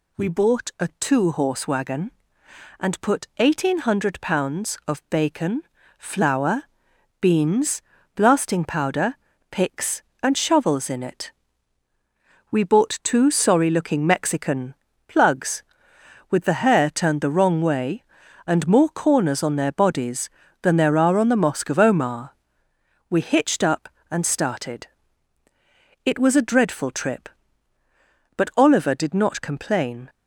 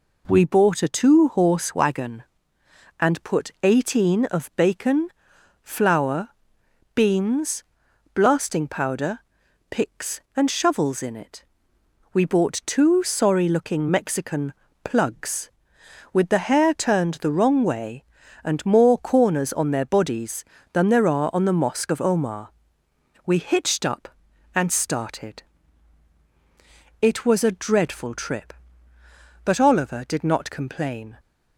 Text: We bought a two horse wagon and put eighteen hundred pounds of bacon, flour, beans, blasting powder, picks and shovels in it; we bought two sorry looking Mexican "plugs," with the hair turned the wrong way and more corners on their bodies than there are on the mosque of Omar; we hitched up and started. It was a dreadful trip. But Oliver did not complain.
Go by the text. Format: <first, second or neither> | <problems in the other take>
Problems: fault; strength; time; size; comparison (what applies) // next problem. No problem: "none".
first | skips "hundred pounds"; at 4.2 s // pauses between "Mexican" and "plugs"; slight; at 14.5 s; 0.28 s long; slight in the first